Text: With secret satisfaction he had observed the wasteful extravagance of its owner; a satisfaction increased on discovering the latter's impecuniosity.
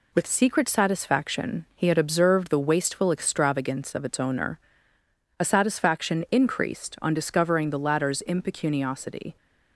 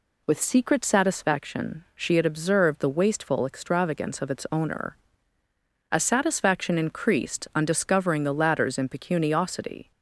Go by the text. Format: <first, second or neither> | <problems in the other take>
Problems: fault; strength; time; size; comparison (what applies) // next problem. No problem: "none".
first | says "she" for "he"; at 1.9 s